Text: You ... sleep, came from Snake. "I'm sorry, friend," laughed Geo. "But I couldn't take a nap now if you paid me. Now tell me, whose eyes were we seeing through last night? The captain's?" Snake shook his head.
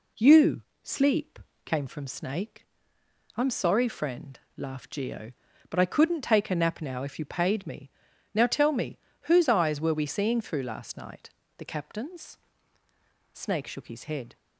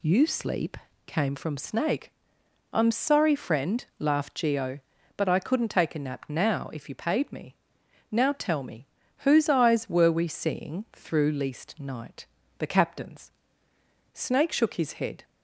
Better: first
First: none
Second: says "least" for "last"; at 11.3 s

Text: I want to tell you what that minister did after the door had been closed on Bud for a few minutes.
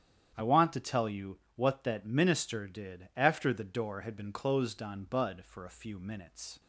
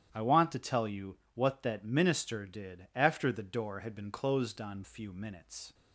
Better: first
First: starts louder than the rest; strong; until 1.5 s; 9.5 dB // pauses between "you" and "what"; slight; at 1.3 s; 0.20 s long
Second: starts louder than the rest; strong; until 1.1 s; 10.5 dB // pauses between "you" and "what"; slight; at 1.1 s; 0.20 s long // skips "Bud for a"; at 4.8 s

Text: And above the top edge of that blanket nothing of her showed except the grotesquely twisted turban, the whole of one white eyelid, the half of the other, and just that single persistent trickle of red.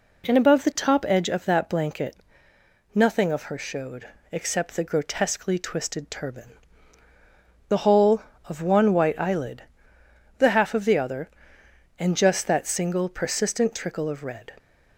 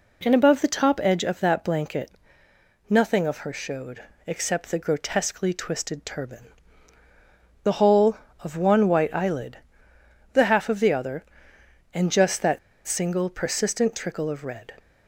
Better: first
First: pauses between "blanket" and "nothing"; noticeable; at 2.1 s; 0.76 s long // pauses between "showed" and "except"; slight; at 4.0 s; 0.22 s long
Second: pauses between "blanket" and "nothing"; noticeable; at 2.1 s; 0.76 s long // pauses between "showed" and "except"; slight; at 4.0 s; 0.22 s long // pauses between "that" and "single"; slight; at 12.5 s; 0.28 s long

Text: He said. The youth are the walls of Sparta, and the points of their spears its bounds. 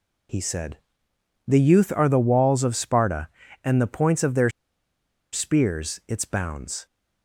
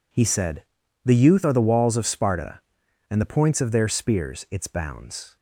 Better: second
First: pauses between "their" and "spears"; noticeable; at 4.4 s; 0.84 s long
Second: none

